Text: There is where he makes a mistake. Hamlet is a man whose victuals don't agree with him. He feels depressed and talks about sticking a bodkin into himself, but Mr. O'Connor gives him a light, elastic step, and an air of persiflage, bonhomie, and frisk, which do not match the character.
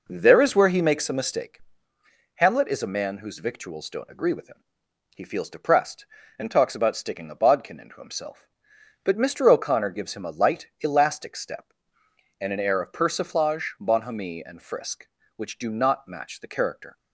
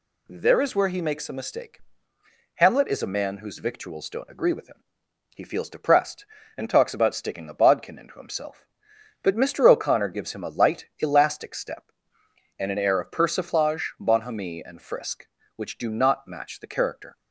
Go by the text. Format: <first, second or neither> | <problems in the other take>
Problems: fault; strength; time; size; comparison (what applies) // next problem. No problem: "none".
second | starts louder than the rest; noticeable; until 1.5 s; 5 dB